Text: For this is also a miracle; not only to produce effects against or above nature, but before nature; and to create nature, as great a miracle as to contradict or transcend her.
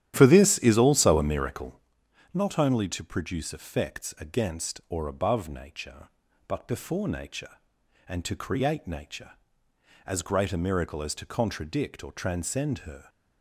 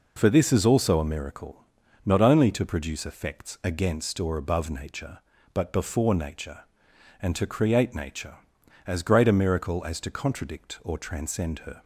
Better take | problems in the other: second | starts louder than the rest; strong; until 1.9 s; 11.5 dB

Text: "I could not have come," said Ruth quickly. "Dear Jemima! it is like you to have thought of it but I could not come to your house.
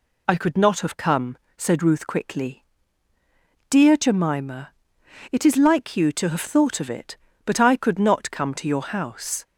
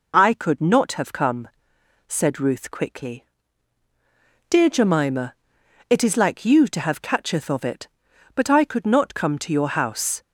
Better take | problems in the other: first | says "catcheth" for "thought"; at 7.0 s

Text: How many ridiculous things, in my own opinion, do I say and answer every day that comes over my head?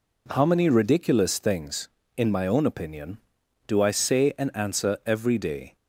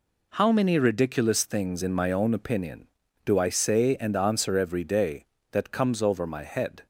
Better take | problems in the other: second | stops before "that comes over my head"; at 5.7 s

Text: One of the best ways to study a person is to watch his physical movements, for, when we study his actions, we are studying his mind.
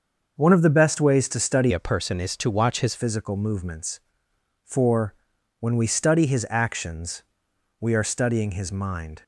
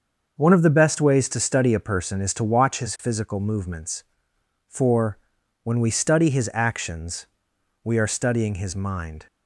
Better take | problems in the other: second | starts louder than the rest; until 1.4 s; 6.5 dB; also in the second // changes voice from "a" to "his"; from 1.7 to 2.9 s; 1.2 s long

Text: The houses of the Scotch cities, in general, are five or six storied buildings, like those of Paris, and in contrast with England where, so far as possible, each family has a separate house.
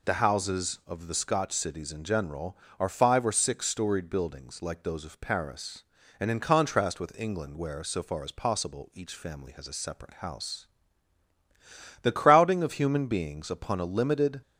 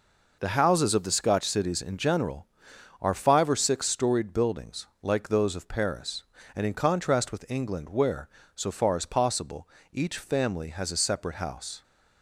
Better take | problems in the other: second | goes on to say "The crowding of human beings upon a limited"; strong; from 12.0 s on; 2.4 s long

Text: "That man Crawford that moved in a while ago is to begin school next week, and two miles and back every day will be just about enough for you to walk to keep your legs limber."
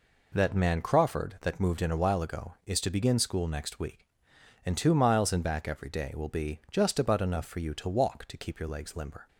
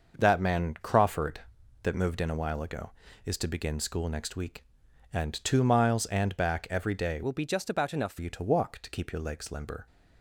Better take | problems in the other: first | starts louder than the rest; noticeable; until 1.1 s; 6 dB // changes voice from "will" to "for"; from 7.2 to 8.1 s; 0.9 s long

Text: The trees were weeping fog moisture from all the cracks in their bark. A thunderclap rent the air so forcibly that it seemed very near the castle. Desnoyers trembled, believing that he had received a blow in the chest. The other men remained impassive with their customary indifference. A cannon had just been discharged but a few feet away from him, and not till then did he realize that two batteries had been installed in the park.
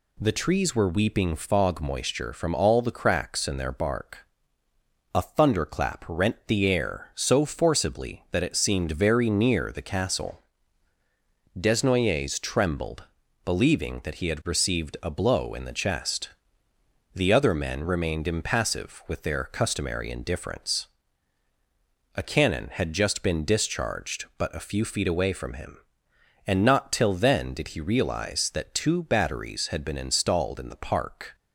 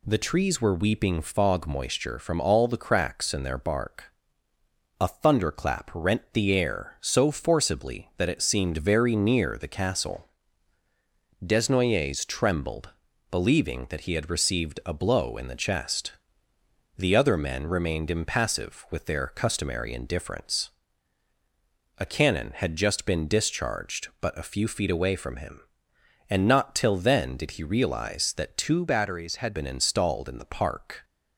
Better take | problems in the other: first | changes voice from "batteries" to "had"; from 28.8 to 29.5 s; 0.7 s long

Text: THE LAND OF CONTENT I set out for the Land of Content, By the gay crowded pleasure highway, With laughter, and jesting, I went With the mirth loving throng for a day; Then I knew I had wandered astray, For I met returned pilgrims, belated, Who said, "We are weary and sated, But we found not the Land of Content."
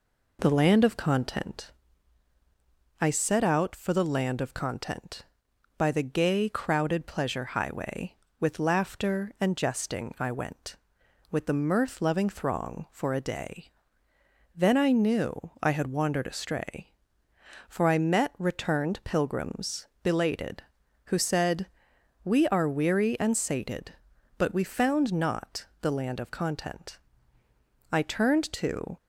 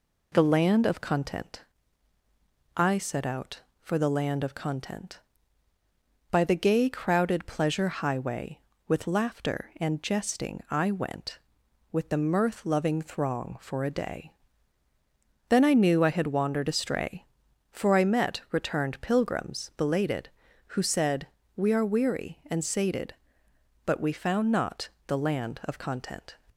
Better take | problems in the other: second | pauses between "CONTENT" and "I"; strong; at 1.7 s; 1.2 s long; also in the second // pauses between "not" and "the"; slight; at 25.6 s; 0.16 s long; slight in the second // goes on to say "I turned to"; noticeable; from 27.9 s on; 1.0 s long

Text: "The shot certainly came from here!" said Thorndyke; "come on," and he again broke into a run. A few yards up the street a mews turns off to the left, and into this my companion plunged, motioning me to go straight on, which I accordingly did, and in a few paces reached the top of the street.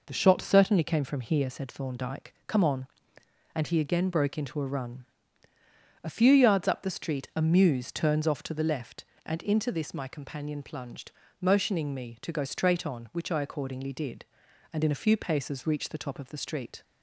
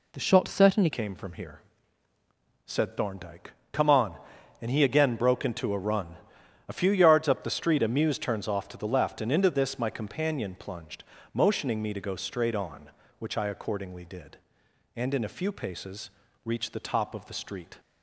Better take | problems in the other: first | changes voice at "came"; from 0.9 s on; 16.8 s long // pauses between "paces" and "reached"; slight; at 16.1 s; 0.32 s long

